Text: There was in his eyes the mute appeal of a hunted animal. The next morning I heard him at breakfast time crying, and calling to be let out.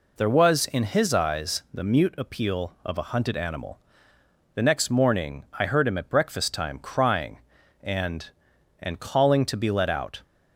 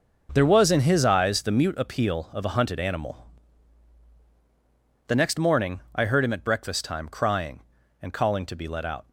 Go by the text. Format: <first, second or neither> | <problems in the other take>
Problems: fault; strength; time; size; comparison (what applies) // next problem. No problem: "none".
second | says "and" twice; at 8.7 s